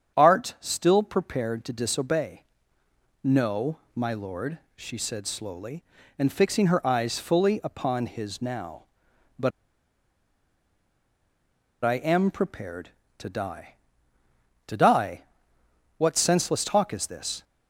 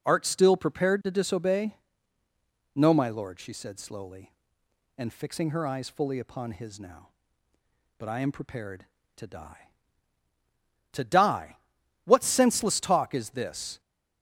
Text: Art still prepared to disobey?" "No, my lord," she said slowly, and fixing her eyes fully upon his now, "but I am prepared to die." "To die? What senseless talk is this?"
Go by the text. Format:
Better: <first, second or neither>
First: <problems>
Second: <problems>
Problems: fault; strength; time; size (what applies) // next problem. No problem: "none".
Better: second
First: starts louder than the rest; strong; until 1.2 s; 8 dB // pauses between "but" and "I"; strong; at 9.5 s; 2.3 s long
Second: none